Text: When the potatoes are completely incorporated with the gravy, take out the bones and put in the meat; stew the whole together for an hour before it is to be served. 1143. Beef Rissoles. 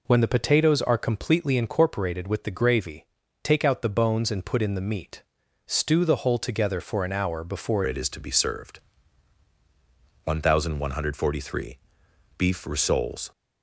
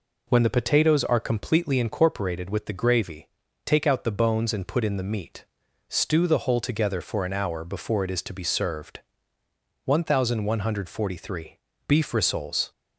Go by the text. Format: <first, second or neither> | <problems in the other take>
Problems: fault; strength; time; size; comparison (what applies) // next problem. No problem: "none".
second | changes voice at "it"; from 7.8 s on; 5.5 s long